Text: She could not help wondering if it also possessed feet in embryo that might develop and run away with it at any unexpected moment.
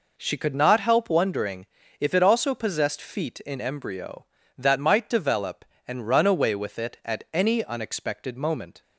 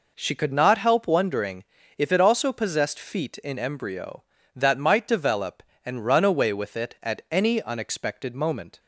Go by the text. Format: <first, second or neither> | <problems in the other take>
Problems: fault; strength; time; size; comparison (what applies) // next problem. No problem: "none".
neither | pauses between "wondering" and "if"; slight; the same in both